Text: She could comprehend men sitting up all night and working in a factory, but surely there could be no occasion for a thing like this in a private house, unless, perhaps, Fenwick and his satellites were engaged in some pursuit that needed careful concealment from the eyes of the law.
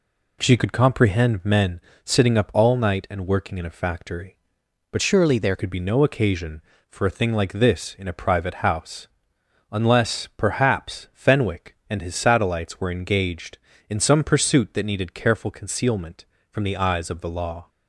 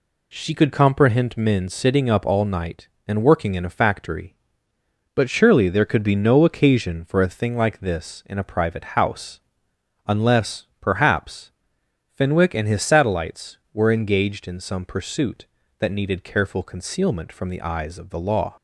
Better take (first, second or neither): second